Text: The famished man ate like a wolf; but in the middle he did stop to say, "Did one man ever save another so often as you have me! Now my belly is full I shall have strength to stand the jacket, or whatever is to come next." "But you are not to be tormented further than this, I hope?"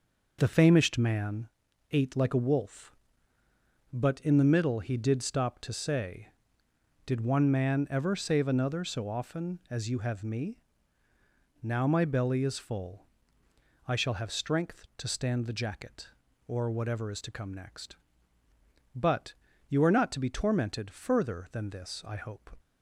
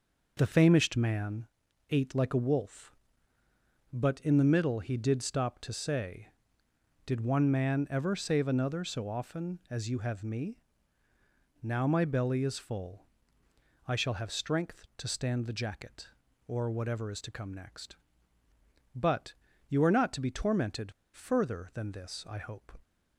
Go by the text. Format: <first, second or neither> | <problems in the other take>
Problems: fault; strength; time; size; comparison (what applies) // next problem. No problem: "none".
first | pauses between "man" and "ate"; at 1.4 s; 0.42 s long; also in the first // pauses between "full" and "I"; noticeable; at 13.0 s; 0.80 s long; noticeable in the first // pauses between "But" and "you"; slight; at 19.3 s; 0.34 s long; slight in the first // pauses between "tormented" and "further"; slight; at 20.9 s; 0.21 s long